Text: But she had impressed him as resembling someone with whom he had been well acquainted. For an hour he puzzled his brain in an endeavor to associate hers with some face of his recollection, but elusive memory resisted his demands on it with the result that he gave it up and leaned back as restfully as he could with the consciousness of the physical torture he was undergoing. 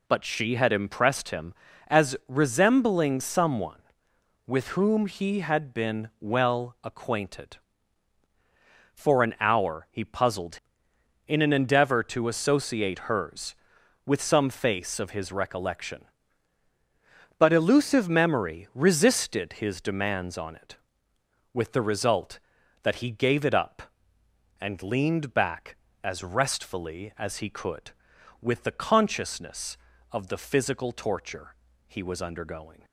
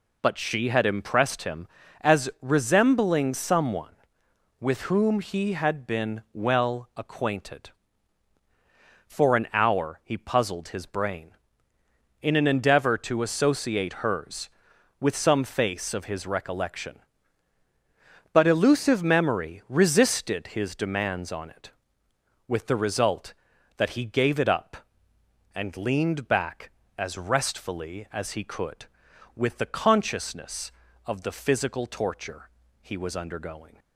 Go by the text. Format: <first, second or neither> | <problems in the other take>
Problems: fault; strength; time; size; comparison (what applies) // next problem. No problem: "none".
second | skips "his brain"; at 10.9 s // pauses between "torture" and "he"; slight; at 31.5 s; 0.32 s long; slight in the second